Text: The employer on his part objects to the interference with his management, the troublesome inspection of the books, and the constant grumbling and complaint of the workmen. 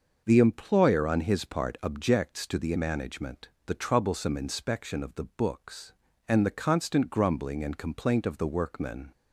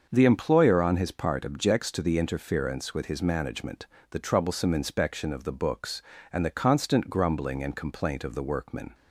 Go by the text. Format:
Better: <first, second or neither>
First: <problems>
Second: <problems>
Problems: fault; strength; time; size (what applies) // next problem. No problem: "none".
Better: second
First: starts louder than the rest; noticeable; until 1.2 s; 6 dB // skips "interference with his"; at 2.7 s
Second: starts louder than the rest; until 1.1 s; 6.5 dB